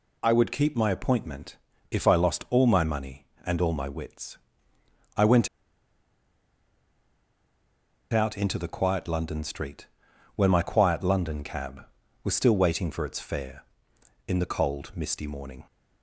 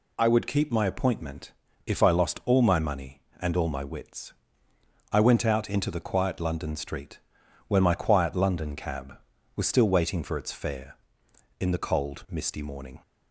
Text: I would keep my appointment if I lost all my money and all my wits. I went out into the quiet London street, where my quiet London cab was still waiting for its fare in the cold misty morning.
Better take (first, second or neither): second